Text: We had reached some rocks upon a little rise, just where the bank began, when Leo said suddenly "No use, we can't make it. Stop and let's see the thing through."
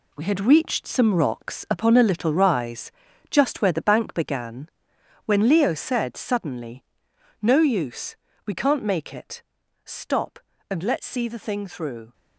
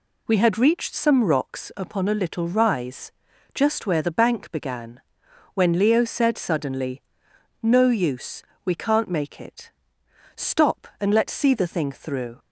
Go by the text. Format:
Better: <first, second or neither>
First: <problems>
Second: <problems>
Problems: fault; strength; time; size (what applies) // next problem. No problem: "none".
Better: second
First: gets quieter; strong; throughout; 7.5 dB // pauses between "suddenly" and "No"; noticeable; at 6.8 s; 0.58 s long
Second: pauses between "suddenly" and "No"; noticeable; at 7.0 s; 0.58 s long